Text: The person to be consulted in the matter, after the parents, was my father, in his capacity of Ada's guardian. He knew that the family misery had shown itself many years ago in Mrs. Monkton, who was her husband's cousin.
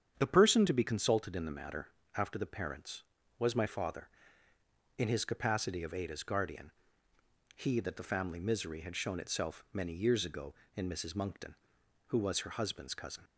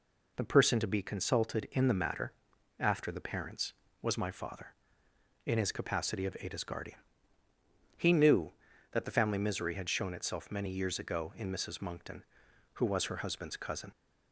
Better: second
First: starts louder than the rest; strong; until 1.1 s; 8.5 dB // skips "knew"; at 7.7 s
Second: none

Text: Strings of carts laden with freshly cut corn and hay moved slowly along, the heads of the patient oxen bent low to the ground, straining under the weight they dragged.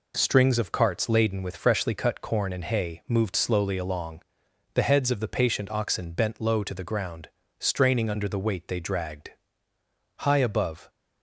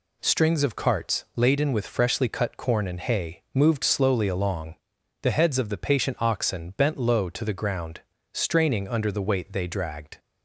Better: second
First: goes on to say "High above"; noticeable; from 10.1 s on; 0.70 s long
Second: none

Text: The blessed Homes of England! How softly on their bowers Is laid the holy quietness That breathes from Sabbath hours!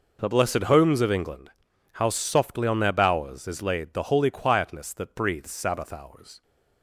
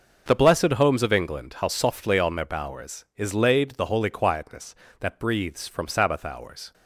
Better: second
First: skips "from"; at 5.4 s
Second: none

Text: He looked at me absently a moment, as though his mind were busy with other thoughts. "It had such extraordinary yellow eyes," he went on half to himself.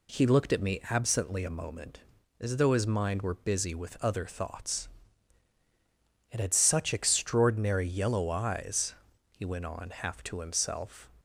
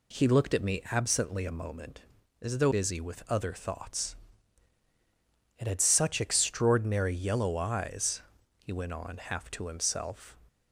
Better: first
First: none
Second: skips "his mind were"; at 2.7 s

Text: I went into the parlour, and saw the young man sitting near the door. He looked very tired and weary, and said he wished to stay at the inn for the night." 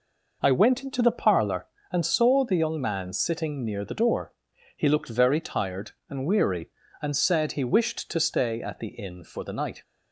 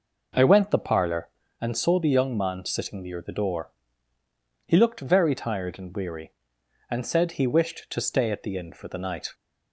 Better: first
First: none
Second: skips "into"; at 0.7 s

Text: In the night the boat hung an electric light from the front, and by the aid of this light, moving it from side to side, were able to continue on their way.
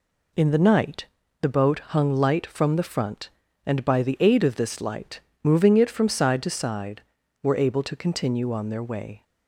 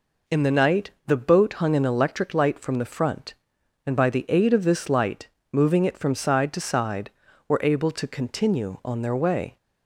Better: second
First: pauses between "night" and "the"; slight; at 1.0 s; 0.36 s long // skips "an electric"; at 2.1 s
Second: pauses between "night" and "the"; slight; at 0.9 s; 0.16 s long

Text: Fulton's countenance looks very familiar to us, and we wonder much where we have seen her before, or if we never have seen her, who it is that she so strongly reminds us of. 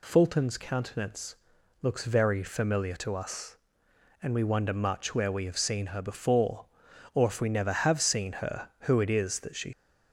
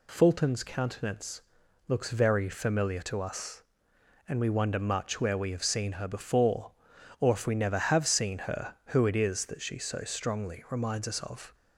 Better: second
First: pauses between "countenance" and "looks"; noticeable; at 1.3 s; 0.46 s long // stops before "so strongly reminds us of"; at 9.7 s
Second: pauses between "countenance" and "looks"; noticeable; at 1.4 s; 0.46 s long

